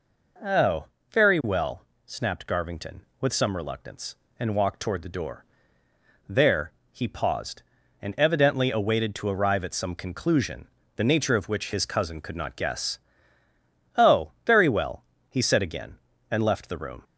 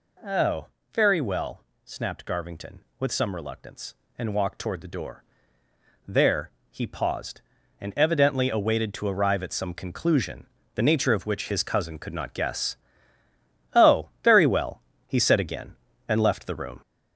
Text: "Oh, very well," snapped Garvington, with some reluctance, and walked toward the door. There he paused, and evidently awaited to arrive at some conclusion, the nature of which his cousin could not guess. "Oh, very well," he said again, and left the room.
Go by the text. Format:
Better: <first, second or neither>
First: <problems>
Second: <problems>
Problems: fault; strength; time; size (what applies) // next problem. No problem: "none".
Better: first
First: pauses between "There" and "he"; slight; at 6.7 s; 0.22 s long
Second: gets louder; noticeable; throughout; 4.5 dB // pauses between "There" and "he"; slight; at 6.4 s; 0.22 s long